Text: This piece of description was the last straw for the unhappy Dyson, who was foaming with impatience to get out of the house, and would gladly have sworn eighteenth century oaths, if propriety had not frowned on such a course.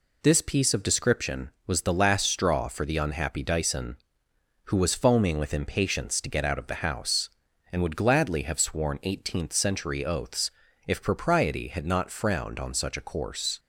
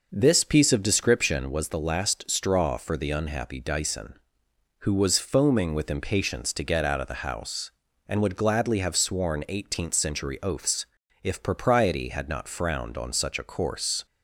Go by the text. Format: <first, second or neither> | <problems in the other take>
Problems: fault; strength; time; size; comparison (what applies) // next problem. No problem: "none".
first | starts louder than the rest; noticeable; until 1.5 s; 5.5 dB